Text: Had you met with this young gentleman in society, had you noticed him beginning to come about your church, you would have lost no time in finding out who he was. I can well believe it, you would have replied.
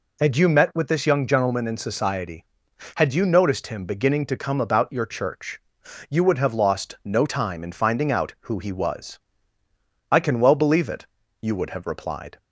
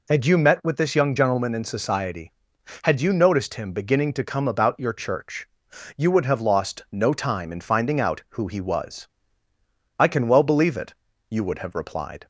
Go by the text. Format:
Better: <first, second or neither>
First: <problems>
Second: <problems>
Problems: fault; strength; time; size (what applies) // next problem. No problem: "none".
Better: neither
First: none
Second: none